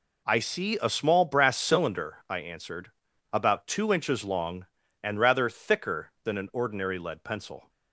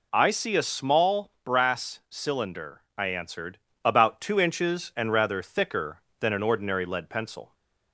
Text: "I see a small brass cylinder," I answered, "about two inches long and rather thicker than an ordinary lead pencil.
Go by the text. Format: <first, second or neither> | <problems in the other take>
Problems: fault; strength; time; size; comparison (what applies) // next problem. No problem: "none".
first | skips "long"; at 4.9 s